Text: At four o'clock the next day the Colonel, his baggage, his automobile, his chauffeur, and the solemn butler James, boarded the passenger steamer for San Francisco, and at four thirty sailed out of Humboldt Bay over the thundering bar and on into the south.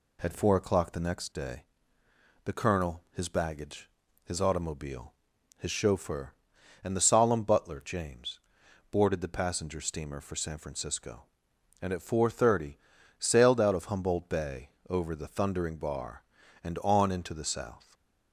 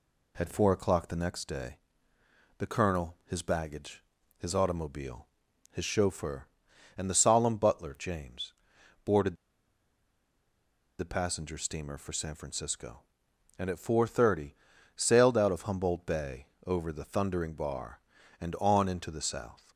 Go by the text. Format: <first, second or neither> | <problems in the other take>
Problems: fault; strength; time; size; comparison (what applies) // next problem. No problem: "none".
first | pauses between "day" and "the"; noticeable; at 1.7 s; 0.80 s long; noticeable in the first // pauses between "boarded" and "the"; strong; at 9.3 s; 1.6 s long // pauses between "thirty" and "sailed"; at 14.5 s; 0.40 s long; also in the first // pauses between "Bay" and "over"; slight; at 16.4 s; 0.20 s long; slight in the first